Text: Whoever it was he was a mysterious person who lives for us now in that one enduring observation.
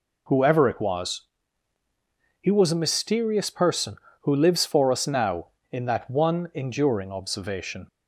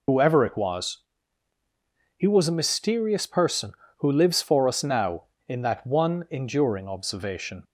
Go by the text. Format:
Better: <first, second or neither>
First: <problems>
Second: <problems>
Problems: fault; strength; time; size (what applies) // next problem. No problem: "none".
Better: first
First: pauses between "was" and "he"; at 1.2 s; 1.2 s long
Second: loses the start of "Whoever"; at 0.0 s; 50 ms // pauses between "was" and "he"; at 0.9 s; 1.2 s long